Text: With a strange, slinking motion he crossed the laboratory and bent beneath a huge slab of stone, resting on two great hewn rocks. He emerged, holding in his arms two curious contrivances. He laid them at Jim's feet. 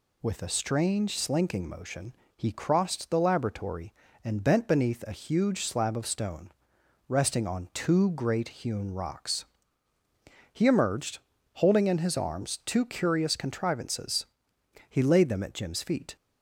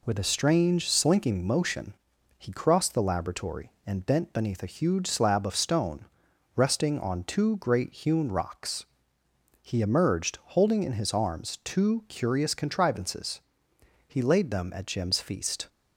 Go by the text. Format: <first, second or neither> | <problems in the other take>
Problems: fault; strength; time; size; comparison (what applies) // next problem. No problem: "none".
first | pauses between "motion" and "he"; at 1.9 s; 0.44 s long; slight in the first // says "feast" for "feet"; at 15.1 s